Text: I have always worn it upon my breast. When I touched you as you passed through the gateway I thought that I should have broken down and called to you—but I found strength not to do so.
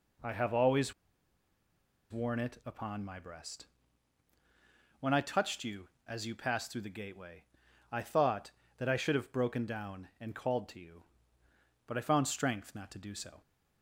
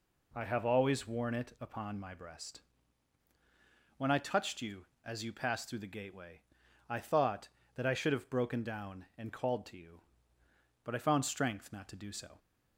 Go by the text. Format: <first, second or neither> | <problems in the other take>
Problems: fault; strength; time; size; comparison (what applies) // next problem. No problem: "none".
second | pauses between "always" and "worn"; at 0.9 s; 1.1 s long // pauses between "gateway" and "I"; noticeable; at 7.4 s; 0.48 s long; noticeable in the second